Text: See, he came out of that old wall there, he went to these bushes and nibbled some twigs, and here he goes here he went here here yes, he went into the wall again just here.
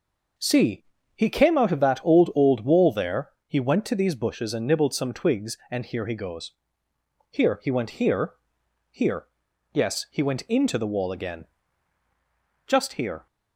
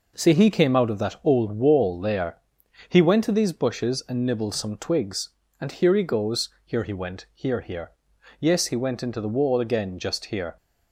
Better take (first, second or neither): second